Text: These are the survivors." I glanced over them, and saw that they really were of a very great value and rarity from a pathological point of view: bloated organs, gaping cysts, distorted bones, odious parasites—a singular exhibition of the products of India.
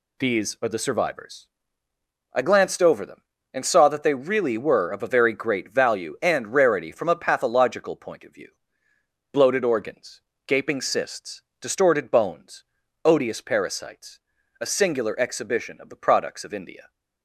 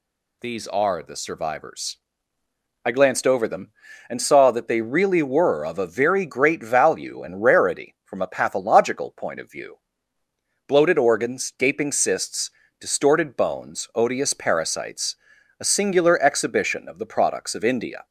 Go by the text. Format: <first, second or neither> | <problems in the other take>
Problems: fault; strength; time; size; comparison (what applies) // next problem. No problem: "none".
neither | none